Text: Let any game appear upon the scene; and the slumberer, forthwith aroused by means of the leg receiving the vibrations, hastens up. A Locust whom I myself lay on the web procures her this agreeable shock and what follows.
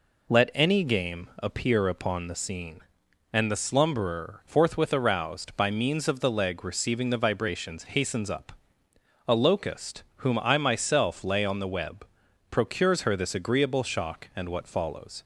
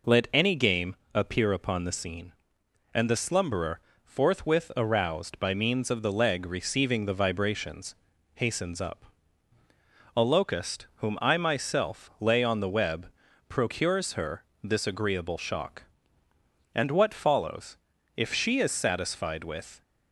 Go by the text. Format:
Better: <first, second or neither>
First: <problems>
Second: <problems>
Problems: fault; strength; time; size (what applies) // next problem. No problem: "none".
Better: first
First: pauses between "web" and "procures"; at 12.0 s; 0.44 s long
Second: pauses between "game" and "appear"; slight; at 0.9 s; 0.20 s long // pauses between "web" and "procures"; at 13.0 s; 0.42 s long // pauses between "her" and "this"; slight; at 14.4 s; 0.20 s long // goes on to say "If she is satisfied with"; from 18.1 s on; 1.6 s long